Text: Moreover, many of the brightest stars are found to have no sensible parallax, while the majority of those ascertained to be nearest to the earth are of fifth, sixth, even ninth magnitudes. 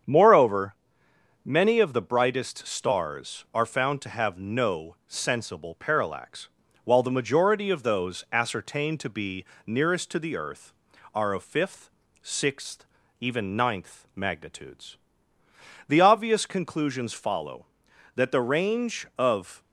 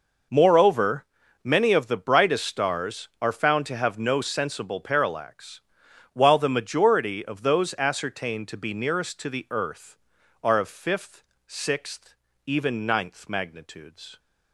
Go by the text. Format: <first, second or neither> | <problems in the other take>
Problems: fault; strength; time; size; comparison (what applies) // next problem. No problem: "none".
second | starts louder than the rest; strong; until 1.7 s; 8 dB // pauses between "be" and "nearest"; slight; at 9.4 s; 0.22 s long // goes on to say "The obvious conclusions follow that the range of"; strong; from 15.8 s on; 3.7 s long